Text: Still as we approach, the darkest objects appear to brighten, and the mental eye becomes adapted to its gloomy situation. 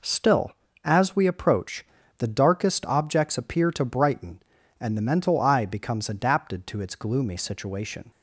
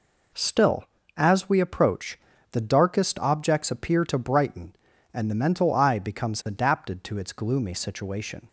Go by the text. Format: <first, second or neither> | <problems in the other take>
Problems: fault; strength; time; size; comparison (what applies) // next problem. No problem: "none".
neither | none